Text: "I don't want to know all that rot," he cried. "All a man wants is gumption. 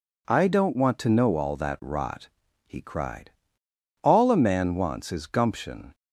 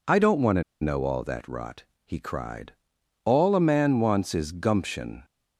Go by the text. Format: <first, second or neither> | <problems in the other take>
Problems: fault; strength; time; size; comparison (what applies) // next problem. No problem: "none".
first | pauses between "to" and "know"; slight; at 0.6 s; 0.18 s long